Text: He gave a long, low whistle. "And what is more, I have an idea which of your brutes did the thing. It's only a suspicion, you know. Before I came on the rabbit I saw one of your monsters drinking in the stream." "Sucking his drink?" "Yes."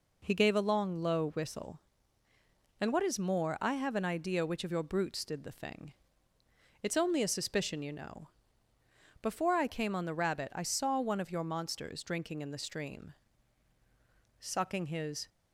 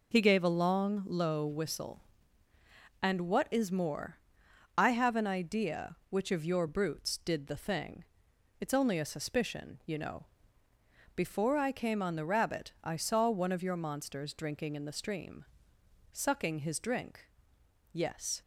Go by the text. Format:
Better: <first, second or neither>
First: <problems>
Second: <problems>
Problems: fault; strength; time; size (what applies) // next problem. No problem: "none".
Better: second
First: stops before "drink Yes"; at 15.2 s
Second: none